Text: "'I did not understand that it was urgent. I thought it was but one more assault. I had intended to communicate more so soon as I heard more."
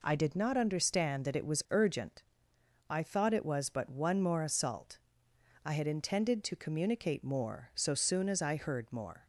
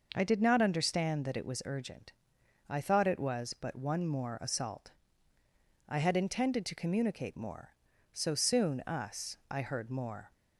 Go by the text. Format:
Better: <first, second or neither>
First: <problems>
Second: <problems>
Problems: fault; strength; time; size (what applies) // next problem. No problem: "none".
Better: first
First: none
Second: says "us" for "as"; at 8.8 s